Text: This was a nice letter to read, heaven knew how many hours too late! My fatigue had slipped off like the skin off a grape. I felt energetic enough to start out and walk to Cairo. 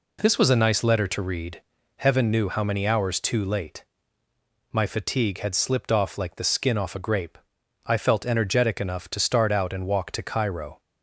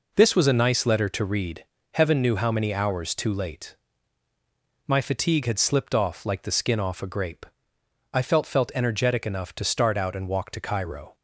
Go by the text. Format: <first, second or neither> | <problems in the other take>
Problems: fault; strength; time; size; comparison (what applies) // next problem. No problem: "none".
first | says "felt" twice; at 8.4 s